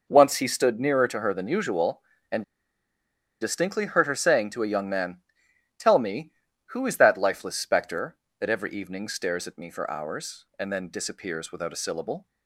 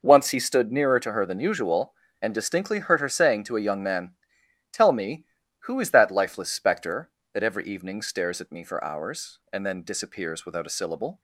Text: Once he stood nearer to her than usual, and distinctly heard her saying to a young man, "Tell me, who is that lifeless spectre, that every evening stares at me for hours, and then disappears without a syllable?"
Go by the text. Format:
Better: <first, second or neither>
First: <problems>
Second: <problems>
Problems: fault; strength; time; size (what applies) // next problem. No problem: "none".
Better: second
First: pauses between "and" and "distinctly"; at 2.4 s; 0.98 s long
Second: none